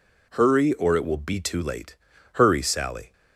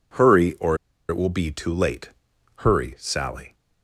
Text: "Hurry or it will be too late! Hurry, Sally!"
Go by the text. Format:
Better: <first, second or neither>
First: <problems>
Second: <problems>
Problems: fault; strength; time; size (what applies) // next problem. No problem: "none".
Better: first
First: none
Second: pauses between "or" and "it"; slight; at 0.7 s; 0.32 s long